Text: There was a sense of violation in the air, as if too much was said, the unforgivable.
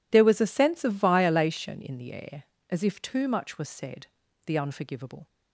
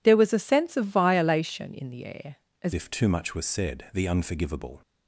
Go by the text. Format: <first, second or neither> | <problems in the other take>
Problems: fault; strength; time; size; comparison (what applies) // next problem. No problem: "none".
first | changes voice at "if"; from 2.7 s on; 2.1 s long